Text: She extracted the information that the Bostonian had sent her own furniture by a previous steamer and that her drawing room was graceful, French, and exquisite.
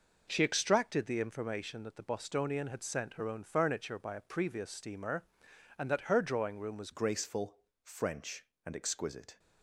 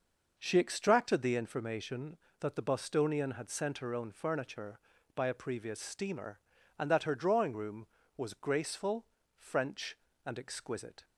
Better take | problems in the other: second | changes voice at "graceful"; from 6.9 s on; 2.4 s long

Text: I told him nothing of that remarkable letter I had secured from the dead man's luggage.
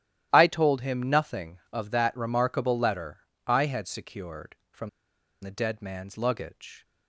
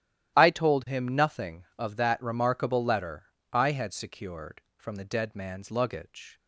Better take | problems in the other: second | starts louder than the rest; strong; until 1.3 s; 12.5 dB; strong in the second // pauses between "letter" and "I"; slight; at 3.1 s; 0.30 s long; slight in the second // pauses between "from" and "the"; noticeable; at 4.8 s; 0.52 s long

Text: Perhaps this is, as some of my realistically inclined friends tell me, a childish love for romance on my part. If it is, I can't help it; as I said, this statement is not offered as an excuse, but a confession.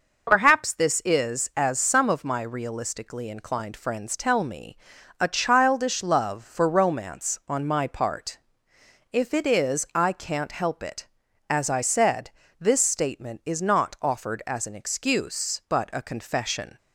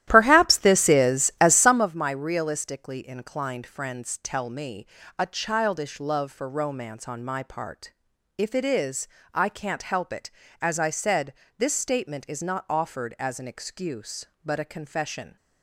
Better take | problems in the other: first | starts louder than the rest; strong; until 1.9 s; 13 dB

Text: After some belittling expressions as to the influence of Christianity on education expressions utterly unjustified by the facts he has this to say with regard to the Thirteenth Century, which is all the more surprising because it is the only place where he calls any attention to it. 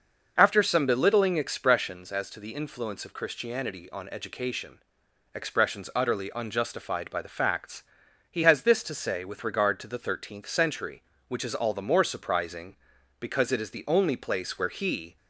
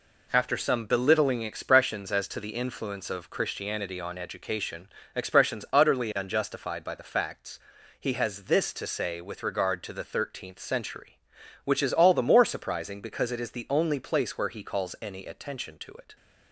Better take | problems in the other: second | starts louder than the rest; noticeable; until 1.3 s; 6 dB // pauses between "education" and "expressions"; noticeable; at 4.8 s; 0.52 s long; slight in the second // pauses between "facts" and "he"; noticeable; at 7.8 s; 0.46 s long; also in the second // stops before "calls any attention to it"; at 15.1 s

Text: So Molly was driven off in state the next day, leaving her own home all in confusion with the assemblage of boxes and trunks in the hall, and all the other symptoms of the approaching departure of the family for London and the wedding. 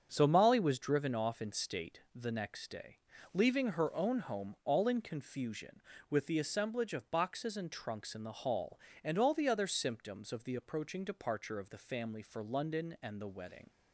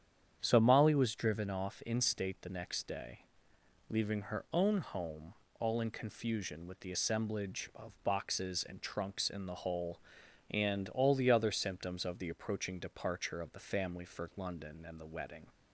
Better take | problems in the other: first | starts louder than the rest; strong; until 1.4 s; 9 dB; strong in the first // pauses between "home" and "all"; slight; at 5.3 s; 0.26 s long // says "hole" for "hall"; at 9.5 s

